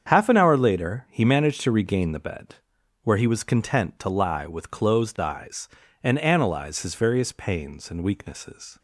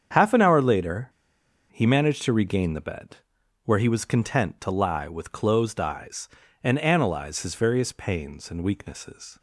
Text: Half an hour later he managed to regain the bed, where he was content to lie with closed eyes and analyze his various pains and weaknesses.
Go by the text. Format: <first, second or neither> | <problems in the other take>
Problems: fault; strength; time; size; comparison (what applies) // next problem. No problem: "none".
first | starts louder than the rest; strong; until 1.7 s; 7.5 dB; strong in the first // pauses between "later" and "he"; noticeable; at 1.0 s; 0.61 s long